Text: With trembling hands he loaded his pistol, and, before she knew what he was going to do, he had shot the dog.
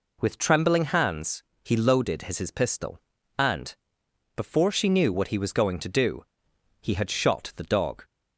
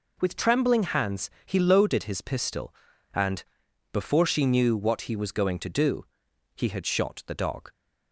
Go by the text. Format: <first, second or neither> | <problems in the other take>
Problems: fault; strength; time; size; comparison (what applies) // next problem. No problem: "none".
second | pauses between "hands" and "he"; slight; at 1.4 s; 0.20 s long; slight in the second // says "his" twice; at 2.3 s